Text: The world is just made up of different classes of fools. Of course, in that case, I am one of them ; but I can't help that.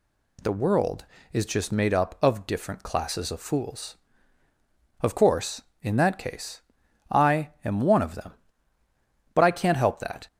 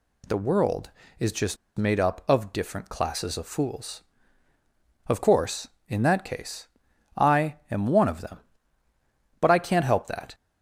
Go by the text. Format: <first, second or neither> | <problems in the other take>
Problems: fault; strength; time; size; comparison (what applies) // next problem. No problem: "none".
first | pauses between "just" and "made"; slight; at 1.5 s; 0.21 s long // pauses between "I" and "am"; slight; at 7.5 s; 0.16 s long; slight in the first